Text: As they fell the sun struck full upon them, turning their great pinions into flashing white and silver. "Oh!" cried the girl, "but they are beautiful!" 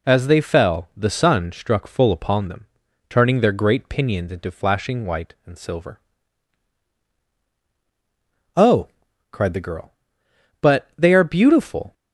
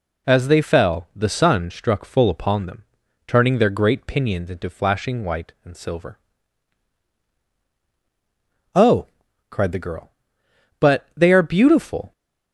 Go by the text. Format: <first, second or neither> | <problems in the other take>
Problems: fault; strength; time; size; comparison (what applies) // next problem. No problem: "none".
neither | none